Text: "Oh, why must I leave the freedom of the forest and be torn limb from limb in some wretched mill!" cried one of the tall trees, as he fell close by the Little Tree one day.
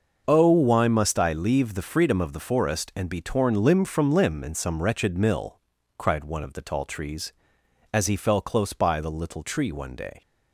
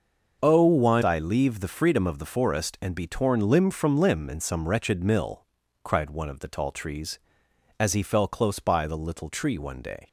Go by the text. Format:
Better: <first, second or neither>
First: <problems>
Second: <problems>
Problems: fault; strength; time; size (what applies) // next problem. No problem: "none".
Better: first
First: starts louder than the rest; noticeable; until 1.2 s; 6 dB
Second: starts louder than the rest; noticeable; until 1.4 s; 6 dB // skips "must"; at 1.0 s